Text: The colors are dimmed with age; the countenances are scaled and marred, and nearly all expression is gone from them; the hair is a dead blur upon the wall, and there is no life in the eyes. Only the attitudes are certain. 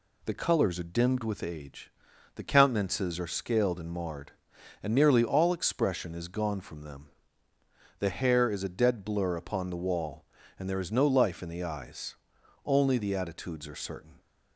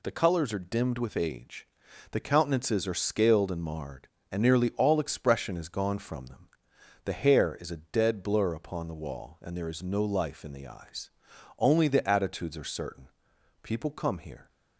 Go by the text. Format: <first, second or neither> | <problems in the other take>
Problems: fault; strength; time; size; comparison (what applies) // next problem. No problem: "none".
first | goes on to say "People come here"; noticeable; from 13.6 s on; 0.88 s long